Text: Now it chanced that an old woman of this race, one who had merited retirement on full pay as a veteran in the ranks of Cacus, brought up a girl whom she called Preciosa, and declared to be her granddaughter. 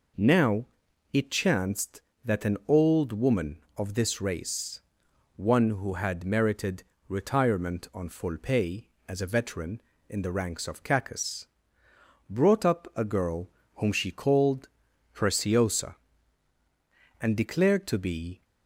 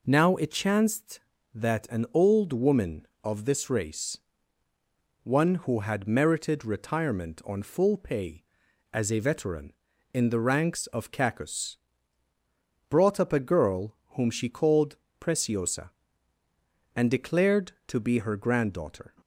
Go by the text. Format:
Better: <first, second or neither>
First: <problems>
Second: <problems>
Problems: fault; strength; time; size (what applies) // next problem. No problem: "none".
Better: second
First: pauses between "Now" and "it"; noticeable; at 0.6 s; 0.46 s long // pauses between "merited" and "retirement"; slight; at 6.8 s; 0.24 s long // pauses between "girl" and "whom"; slight; at 13.4 s; 0.26 s long // pauses between "called" and "Preciosa"; noticeable; at 14.6 s; 0.46 s long // stops before "her granddaughter"; at 18.4 s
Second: pauses between "called" and "Preciosa"; slight; at 14.9 s; 0.24 s long